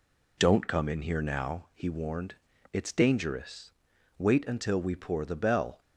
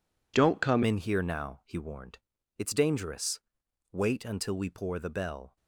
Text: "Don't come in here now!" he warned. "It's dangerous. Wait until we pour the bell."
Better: first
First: none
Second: changes voice at "in"; from 0.8 s on; 4.7 s long

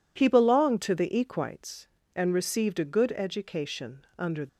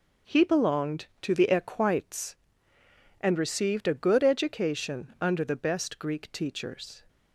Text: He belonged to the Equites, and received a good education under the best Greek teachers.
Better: second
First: stops before "the best Greek teachers"; at 4.4 s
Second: none

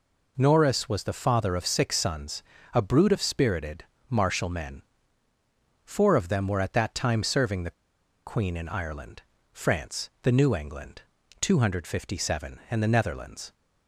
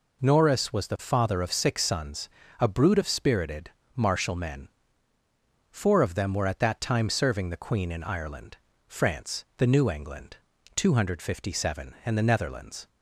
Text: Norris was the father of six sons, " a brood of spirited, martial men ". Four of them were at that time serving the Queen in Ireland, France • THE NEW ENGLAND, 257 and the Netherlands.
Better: second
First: pauses between "the" and "Queen"; noticeable; at 7.7 s; 0.54 s long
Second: none

